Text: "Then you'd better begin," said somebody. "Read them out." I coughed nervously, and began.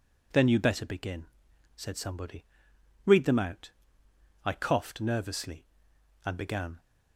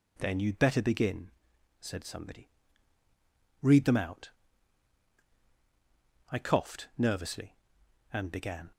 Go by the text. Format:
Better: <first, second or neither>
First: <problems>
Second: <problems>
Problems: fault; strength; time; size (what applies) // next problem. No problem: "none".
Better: neither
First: none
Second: none